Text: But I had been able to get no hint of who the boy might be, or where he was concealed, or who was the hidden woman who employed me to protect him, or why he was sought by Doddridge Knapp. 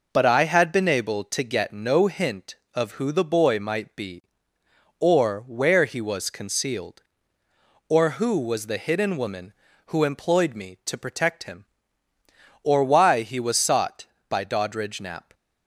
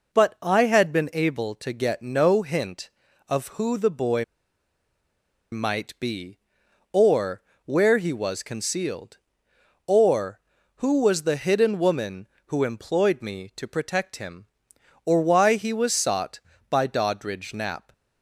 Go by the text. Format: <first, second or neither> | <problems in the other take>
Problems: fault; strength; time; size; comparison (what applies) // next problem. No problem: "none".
first | pauses between "boy" and "might"; strong; at 4.2 s; 1.2 s long // pauses between "or" and "where"; slight; at 7.4 s; 0.24 s long